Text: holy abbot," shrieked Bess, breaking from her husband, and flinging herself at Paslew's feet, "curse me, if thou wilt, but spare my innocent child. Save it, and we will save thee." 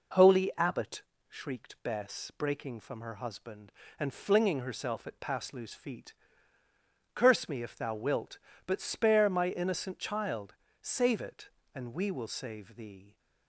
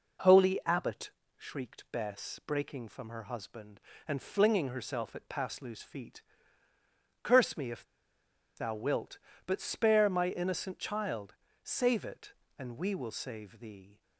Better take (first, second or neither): first